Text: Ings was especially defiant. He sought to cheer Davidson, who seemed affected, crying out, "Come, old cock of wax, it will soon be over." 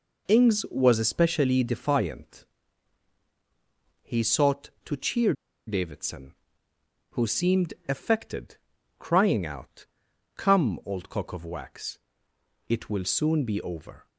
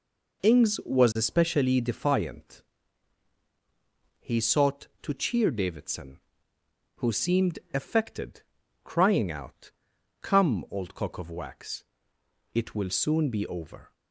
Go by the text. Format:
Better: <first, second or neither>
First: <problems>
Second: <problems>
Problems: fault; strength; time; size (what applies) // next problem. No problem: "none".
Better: second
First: pauses between "cheer" and "Davidson"; slight; at 5.3 s; 0.33 s long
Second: none